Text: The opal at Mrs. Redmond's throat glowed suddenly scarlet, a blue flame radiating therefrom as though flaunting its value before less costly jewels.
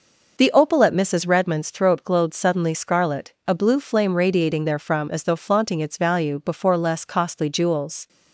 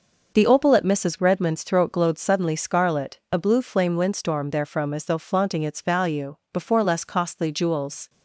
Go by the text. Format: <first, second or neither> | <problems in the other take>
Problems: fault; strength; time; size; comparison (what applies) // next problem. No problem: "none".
first | says "windstorm" for "radiating"; at 3.9 s // pauses between "value" and "before"; slight; at 6.3 s; 0.18 s long